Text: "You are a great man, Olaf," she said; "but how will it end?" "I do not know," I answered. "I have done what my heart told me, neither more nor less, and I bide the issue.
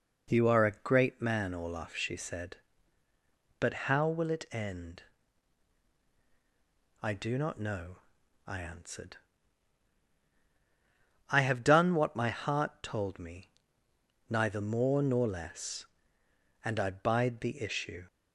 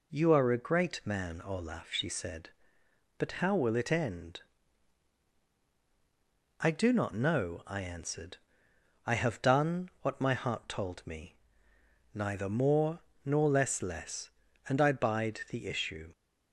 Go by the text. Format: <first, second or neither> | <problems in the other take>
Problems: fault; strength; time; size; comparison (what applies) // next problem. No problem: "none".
first | pauses between "more" and "nor"; slight; at 13.0 s; 0.22 s long // says "less" twice; at 13.8 s